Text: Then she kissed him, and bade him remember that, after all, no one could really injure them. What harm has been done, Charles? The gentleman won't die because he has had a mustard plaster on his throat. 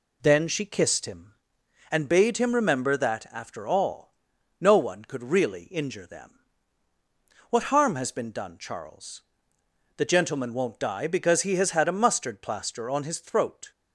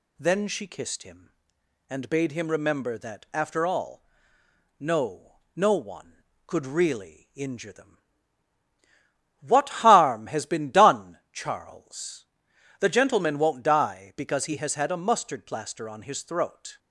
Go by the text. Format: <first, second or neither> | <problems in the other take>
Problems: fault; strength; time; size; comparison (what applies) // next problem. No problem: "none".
first | says "no" twice; at 5.5 s